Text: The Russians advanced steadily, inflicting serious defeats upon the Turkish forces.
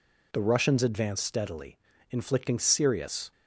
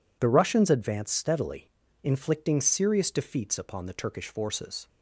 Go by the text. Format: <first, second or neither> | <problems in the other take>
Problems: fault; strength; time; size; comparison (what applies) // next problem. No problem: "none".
second | stops before "defeats upon the Turkish forces"; at 3.3 s